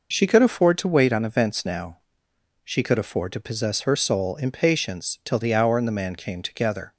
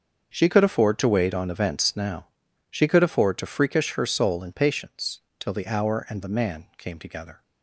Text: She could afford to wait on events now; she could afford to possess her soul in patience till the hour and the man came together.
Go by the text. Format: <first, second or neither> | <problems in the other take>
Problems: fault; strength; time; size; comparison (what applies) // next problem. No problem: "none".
first | starts louder than the rest; until 1.3 s; 6.5 dB // says "freakish" for "possess"; at 3.4 s // pauses between "patience" and "till"; slight; at 5.2 s; 0.18 s long